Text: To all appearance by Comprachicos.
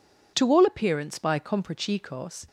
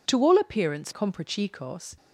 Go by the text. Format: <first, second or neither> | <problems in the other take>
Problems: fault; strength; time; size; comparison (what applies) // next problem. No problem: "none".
first | skips "by"; at 0.9 s